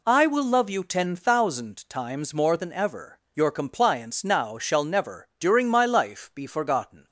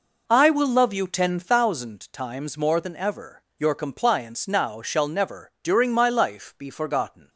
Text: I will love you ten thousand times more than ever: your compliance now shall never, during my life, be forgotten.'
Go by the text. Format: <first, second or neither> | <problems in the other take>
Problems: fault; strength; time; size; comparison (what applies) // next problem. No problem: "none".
first | starts louder than the rest; noticeable; until 1.7 s; 5 dB